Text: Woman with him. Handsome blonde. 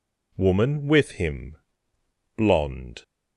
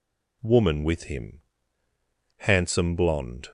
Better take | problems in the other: second | skips "Handsome"; at 1.9 s

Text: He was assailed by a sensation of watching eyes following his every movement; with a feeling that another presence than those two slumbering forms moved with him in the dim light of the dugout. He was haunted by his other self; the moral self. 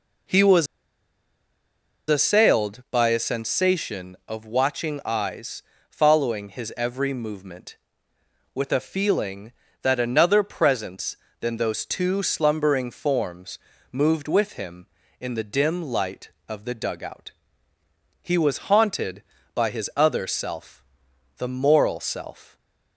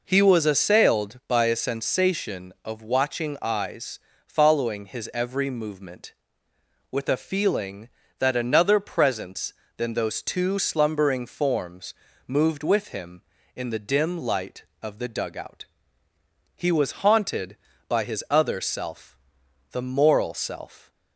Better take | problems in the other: second | pauses between "was" and "assailed"; strong; at 0.6 s; 1.4 s long // pauses between "eyes" and "following"; slight; at 5.6 s; 0.26 s long; slight in the second // pauses between "forms" and "moved"; slight; at 13.5 s; 0.32 s long; slight in the second

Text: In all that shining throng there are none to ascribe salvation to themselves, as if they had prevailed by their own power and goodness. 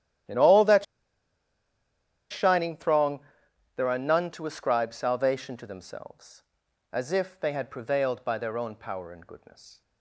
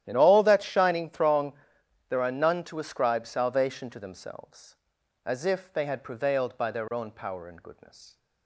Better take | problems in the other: second | starts louder than the rest; strong; until 2.7 s; 12 dB; strong in the second // pauses between "that" and "shining"; strong; at 0.8 s; 1.4 s long // pauses between "throng" and "there"; noticeable; at 3.1 s; 0.56 s long; noticeable in the second

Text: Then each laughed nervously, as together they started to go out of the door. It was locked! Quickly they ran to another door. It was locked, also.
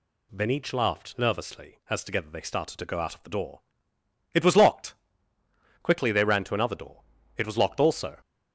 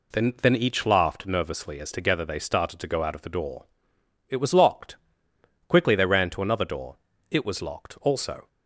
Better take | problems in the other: first | says "Then" twice; at 0.4 s

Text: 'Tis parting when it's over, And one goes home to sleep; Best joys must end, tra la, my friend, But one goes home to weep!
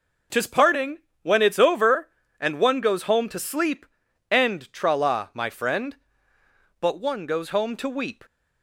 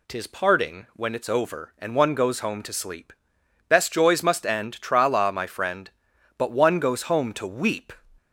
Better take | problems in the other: second | pauses between "parting" and "when"; slight; at 0.9 s; 0.24 s long // skips "Best joys must"; at 4.0 s

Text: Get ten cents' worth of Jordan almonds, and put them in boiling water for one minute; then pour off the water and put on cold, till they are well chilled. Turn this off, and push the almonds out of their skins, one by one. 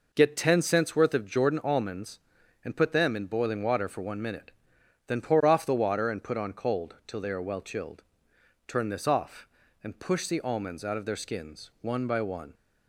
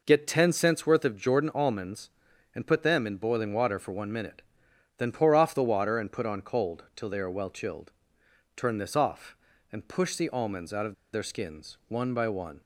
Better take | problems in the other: first | pauses between "of" and "their"; slight; at 10.9 s; 0.18 s long

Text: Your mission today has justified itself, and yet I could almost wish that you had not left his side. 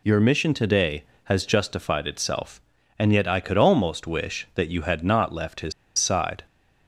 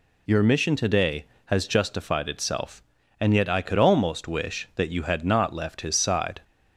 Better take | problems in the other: second | pauses between "his" and "side"; slight; at 5.7 s; 0.25 s long

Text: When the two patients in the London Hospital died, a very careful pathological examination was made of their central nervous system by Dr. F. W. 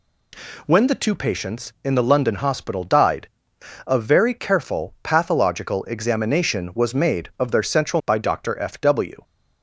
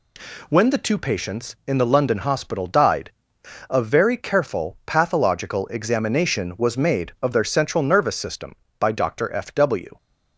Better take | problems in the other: second | skips "nervous system"; at 8.0 s

